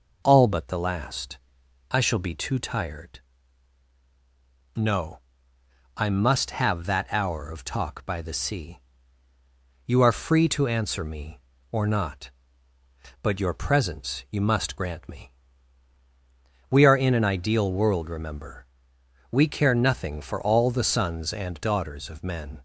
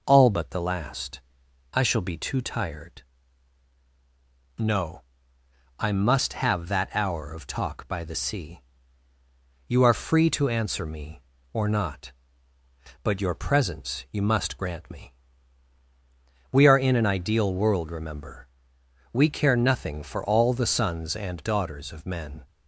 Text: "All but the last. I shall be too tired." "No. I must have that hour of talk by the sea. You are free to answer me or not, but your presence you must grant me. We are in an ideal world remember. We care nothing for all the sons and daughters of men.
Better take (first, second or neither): neither